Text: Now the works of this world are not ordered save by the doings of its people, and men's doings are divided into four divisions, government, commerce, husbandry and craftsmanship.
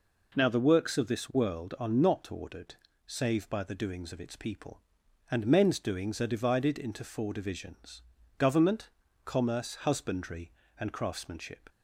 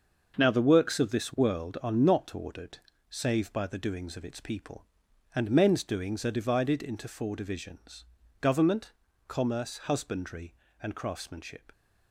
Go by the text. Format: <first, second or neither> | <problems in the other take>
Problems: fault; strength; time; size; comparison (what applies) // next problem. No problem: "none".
first | gets quieter; strong; throughout; 8.5 dB // pauses between "ordered" and "save"; slight; at 2.7 s; 0.30 s long; slight in the first